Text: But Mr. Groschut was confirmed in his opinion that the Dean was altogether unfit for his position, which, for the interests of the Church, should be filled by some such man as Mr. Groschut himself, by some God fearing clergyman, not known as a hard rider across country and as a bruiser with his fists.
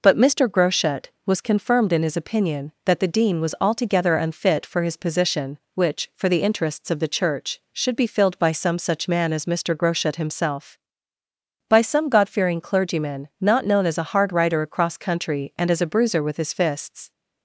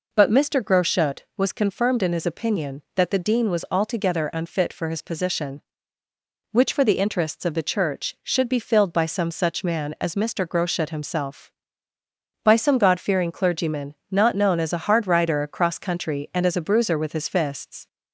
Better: neither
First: none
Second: none

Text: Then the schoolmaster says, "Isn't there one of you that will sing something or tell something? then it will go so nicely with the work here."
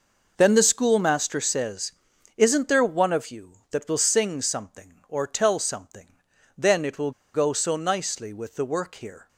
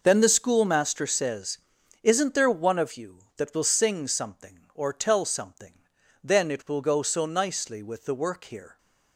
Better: second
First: pauses between "will" and "go"; slight; at 7.1 s; 0.23 s long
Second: none

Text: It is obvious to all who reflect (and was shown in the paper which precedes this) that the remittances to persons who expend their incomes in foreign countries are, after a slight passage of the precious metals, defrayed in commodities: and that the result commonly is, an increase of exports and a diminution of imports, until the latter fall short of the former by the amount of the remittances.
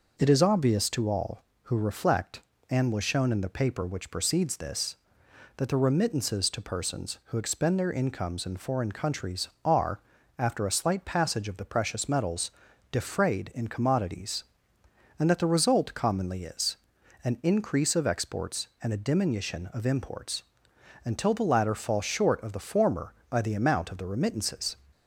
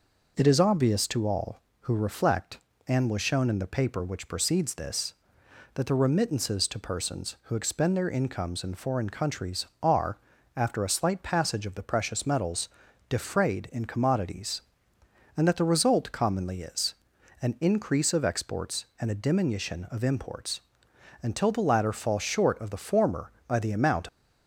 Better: first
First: none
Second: stops before "of the remittances"; at 24.0 s

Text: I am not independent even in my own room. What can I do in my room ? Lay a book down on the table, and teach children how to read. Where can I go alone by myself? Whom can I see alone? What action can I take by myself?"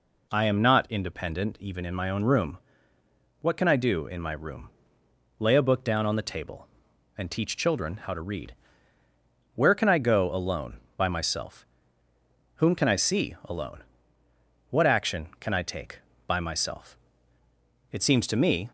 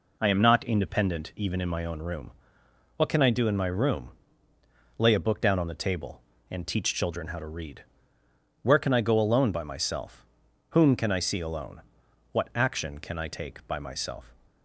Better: second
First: goes on to say "It seems to me"; noticeable; from 17.8 s on; 0.78 s long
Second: none

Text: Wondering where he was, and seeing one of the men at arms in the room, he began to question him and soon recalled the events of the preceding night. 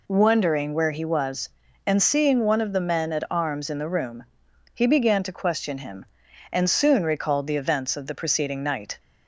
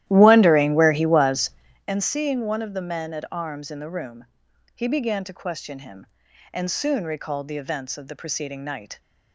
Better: first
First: none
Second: starts louder than the rest; strong; until 1.9 s; 13.5 dB

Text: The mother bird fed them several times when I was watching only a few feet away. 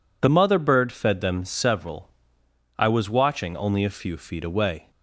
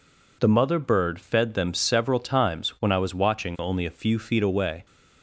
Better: second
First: skips "times when"; at 2.4 s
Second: none

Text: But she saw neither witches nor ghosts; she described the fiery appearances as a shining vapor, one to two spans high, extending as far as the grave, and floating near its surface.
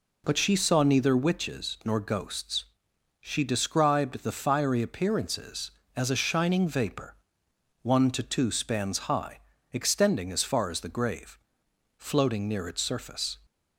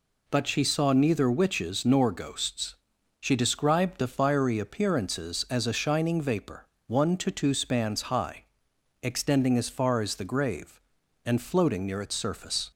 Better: second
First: skips "and"; at 11.6 s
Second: none

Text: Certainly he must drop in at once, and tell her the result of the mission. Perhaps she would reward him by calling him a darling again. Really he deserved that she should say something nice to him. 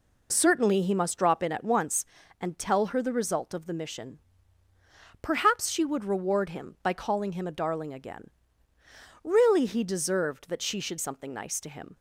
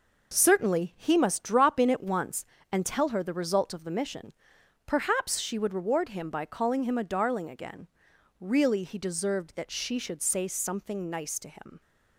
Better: second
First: skips "say"; at 10.9 s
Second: none

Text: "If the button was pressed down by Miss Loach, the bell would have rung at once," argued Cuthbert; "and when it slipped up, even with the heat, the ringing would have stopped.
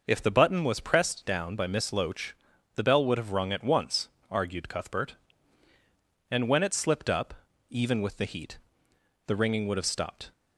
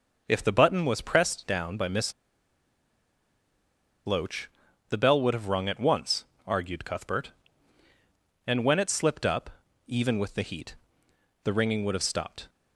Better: first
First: none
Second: pauses between "Miss" and "Loach"; strong; at 2.1 s; 1.9 s long

